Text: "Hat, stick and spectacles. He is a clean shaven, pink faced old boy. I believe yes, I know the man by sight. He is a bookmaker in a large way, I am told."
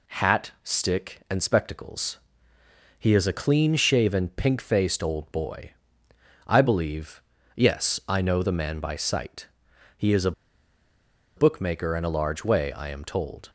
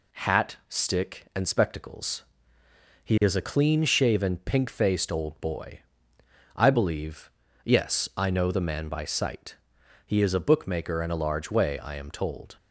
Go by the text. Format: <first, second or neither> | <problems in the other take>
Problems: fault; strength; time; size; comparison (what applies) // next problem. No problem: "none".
second | pauses between "believe" and "yes"; slight; at 7.2 s; 0.34 s long; slight in the second // pauses between "a" and "bookmaker"; at 10.3 s; 1.0 s long